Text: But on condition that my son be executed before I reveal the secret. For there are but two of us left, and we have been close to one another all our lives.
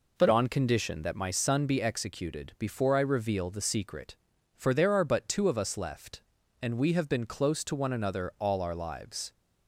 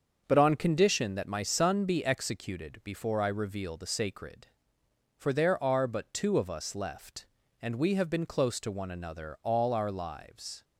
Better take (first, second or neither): first